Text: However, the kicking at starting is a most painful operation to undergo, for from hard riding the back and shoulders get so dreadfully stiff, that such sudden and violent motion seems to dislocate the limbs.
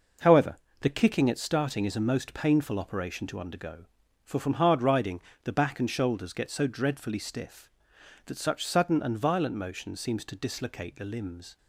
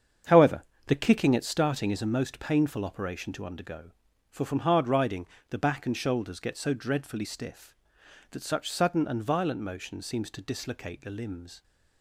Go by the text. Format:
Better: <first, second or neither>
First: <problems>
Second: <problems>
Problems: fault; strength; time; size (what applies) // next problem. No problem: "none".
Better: first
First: pauses between "riding" and "the"; slight; at 5.2 s; 0.24 s long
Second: starts louder than the rest; strong; until 2.1 s; 7.5 dB // pauses between "riding" and "the"; slight; at 5.2 s; 0.24 s long